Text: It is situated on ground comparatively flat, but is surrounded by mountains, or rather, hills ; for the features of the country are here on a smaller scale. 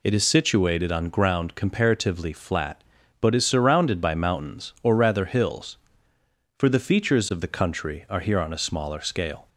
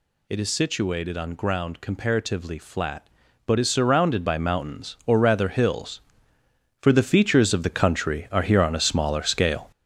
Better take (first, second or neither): first